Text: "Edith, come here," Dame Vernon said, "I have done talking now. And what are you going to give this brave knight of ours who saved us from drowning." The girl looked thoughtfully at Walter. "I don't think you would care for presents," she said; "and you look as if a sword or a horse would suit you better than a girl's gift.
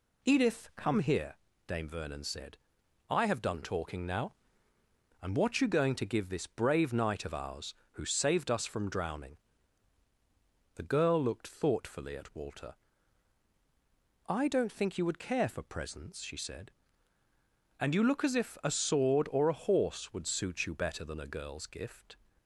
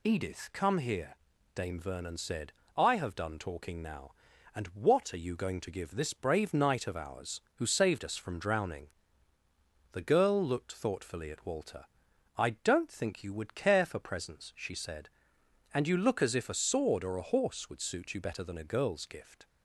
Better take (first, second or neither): second